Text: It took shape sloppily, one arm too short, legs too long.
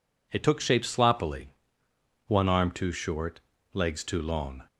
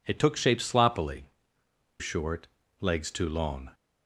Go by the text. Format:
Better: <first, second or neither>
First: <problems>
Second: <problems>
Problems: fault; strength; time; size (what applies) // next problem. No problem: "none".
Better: first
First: none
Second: skips "one arm too"; at 1.6 s